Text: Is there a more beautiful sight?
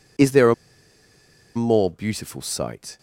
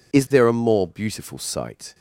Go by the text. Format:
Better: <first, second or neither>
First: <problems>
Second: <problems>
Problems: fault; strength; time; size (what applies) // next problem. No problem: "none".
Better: second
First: pauses between "a" and "more"; at 0.5 s; 1.0 s long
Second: none